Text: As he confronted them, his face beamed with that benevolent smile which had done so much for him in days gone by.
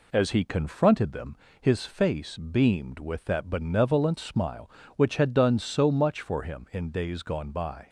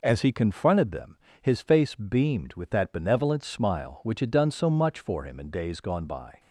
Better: neither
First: none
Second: none

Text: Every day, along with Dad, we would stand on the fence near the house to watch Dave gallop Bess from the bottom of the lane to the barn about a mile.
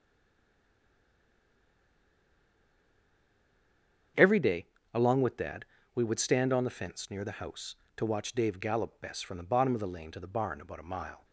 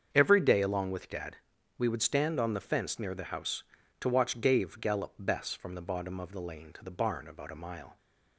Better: second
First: stays silent before the first word; strong; until 4.1 s; 4.1 s long // starts louder than the rest; strong; until 5.4 s; 7.5 dB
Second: starts louder than the rest; strong; until 1.1 s; 7.5 dB

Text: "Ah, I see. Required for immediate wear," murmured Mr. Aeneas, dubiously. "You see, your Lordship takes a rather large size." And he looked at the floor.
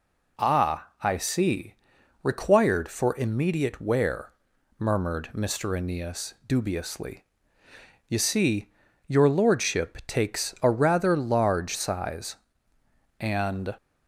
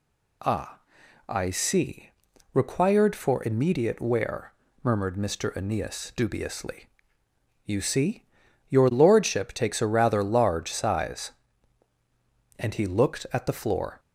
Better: second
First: stops before "he looked at the floor"; at 13.7 s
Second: none

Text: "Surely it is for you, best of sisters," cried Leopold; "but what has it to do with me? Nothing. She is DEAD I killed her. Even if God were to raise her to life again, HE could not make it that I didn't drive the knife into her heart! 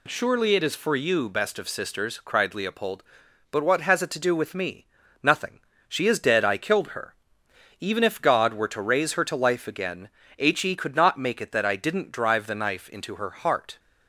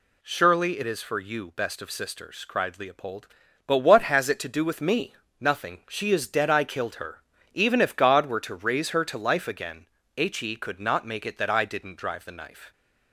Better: first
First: none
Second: stops before "into her heart"; at 12.7 s

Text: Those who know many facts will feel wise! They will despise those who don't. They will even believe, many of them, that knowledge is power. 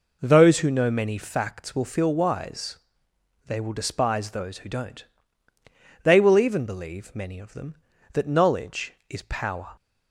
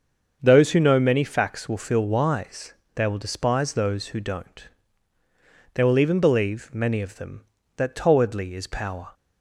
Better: first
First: none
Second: starts louder than the rest; until 1.4 s; 7 dB // says "towardly" for "knowledge"; at 7.9 s

